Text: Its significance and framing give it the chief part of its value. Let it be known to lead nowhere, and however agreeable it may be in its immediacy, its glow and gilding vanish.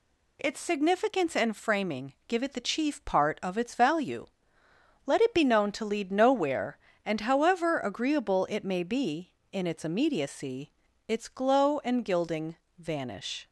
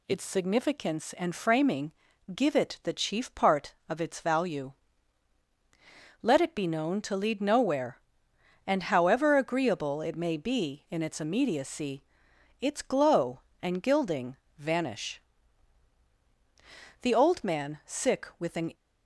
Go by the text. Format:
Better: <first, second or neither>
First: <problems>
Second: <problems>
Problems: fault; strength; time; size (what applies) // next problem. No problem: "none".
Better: first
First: pauses between "gilding" and "vanish"; slight; at 12.5 s; 0.22 s long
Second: pauses between "framing" and "give"; at 1.9 s; 0.42 s long // pauses between "gilding" and "vanish"; slight; at 14.3 s; 0.20 s long // goes on to say "The old man sick with an"; strong; from 17.0 s on; 1.7 s long